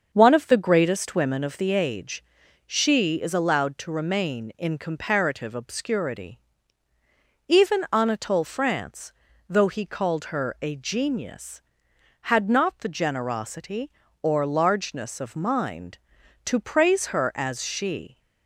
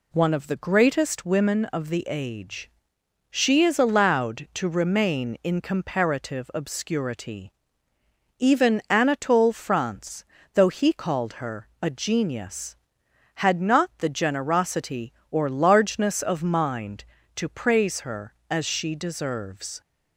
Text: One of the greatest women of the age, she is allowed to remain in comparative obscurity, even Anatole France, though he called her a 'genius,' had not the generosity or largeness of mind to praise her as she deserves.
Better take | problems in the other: second | starts louder than the rest; until 1.1 s; 6.5 dB // stops before "deserves"; at 18.1 s

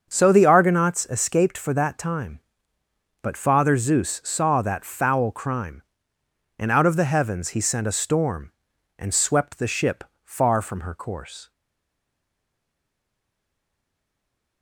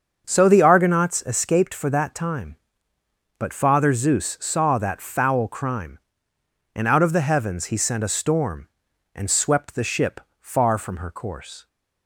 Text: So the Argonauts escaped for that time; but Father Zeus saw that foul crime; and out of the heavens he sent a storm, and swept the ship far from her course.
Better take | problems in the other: second | starts louder than the rest; until 1.1 s; 7 dB; also in the second // pauses between "ship" and "far"; slight; at 10.0 s; 0.20 s long; slight in the second // stays silent after the last word; strong; from 11.5 s on; 3.1 s long

